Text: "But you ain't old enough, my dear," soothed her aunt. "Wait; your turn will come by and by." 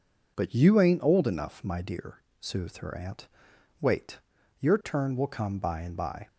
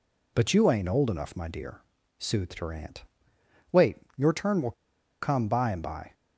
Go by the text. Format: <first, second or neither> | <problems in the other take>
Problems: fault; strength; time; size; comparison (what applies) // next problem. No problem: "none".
first | pauses between "will" and "come"; noticeable; at 4.7 s; 0.49 s long